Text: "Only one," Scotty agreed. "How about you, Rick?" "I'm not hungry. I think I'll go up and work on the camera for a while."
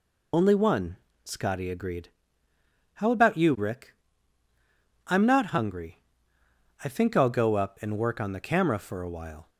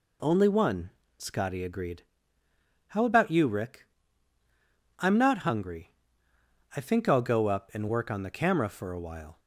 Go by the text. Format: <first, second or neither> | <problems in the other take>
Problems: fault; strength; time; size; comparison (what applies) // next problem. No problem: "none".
second | loses the start of "Only"; at 0.3 s; 70 ms